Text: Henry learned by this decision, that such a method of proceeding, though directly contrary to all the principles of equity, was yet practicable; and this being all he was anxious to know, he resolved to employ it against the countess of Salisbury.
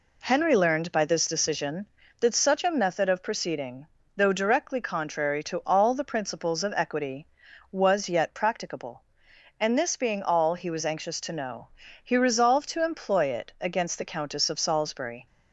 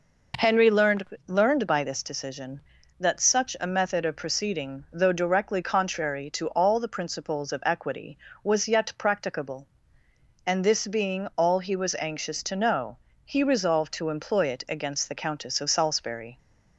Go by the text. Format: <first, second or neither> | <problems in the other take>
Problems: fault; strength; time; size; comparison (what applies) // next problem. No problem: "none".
first | says "learned" twice; at 1.2 s